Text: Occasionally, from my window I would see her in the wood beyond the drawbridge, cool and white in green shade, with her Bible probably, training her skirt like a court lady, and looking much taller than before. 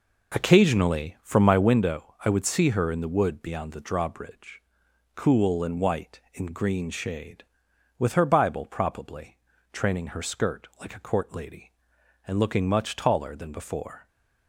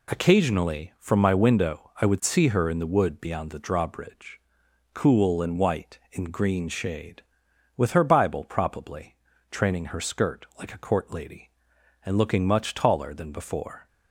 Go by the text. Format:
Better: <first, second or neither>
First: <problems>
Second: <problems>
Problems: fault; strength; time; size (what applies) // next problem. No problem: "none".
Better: second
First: starts louder than the rest; noticeable; until 1.7 s; 5 dB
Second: none